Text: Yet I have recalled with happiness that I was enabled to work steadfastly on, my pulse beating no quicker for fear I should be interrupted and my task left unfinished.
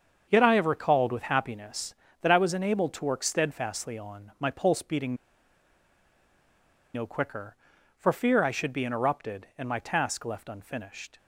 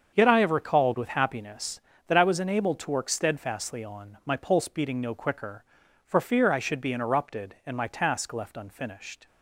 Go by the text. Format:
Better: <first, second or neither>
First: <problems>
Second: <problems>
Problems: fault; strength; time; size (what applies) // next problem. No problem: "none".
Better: second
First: starts louder than the rest; until 1.3 s; 7 dB // pauses between "beating" and "no"; strong; at 5.1 s; 1.8 s long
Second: starts louder than the rest; until 1.1 s; 7 dB